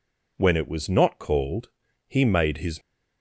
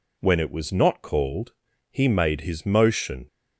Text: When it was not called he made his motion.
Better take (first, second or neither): second